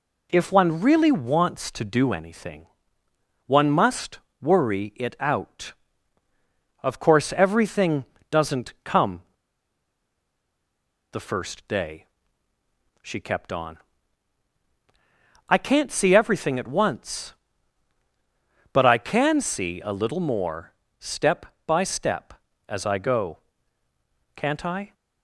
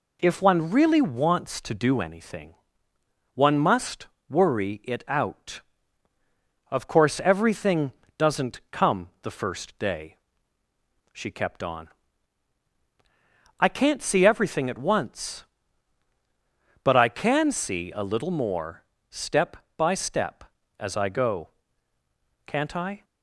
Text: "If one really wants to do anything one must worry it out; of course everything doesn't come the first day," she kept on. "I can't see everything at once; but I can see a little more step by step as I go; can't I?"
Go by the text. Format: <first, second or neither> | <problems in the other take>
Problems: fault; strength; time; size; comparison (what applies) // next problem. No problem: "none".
second | pauses between "anything" and "one"; noticeable; at 2.6 s; 0.80 s long; noticeable in the second // pauses between "must" and "worry"; slight; at 4.1 s; 0.22 s long; slight in the second // pauses between "everything" and "doesn't"; slight; at 8.0 s; 0.26 s long; slight in the second // pauses between "come" and "the"; strong; at 9.2 s; 1.8 s long // pauses between "more" and "step"; slight; at 20.7 s; 0.26 s long; slight in the second